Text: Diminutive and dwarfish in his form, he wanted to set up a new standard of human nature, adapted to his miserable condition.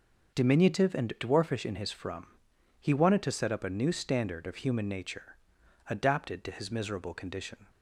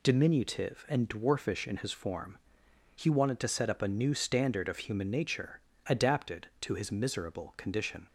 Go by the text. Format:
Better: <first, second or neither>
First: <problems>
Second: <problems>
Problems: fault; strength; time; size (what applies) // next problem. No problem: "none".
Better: second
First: starts louder than the rest; until 1.4 s; 6.5 dB // says "from" for "form"; at 1.9 s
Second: none